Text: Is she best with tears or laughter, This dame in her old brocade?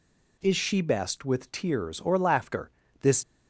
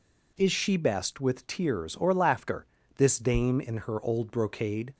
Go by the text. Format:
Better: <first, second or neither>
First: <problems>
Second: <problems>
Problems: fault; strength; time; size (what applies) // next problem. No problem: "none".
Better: second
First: stops before "dame in her old brocade"; at 3.2 s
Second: none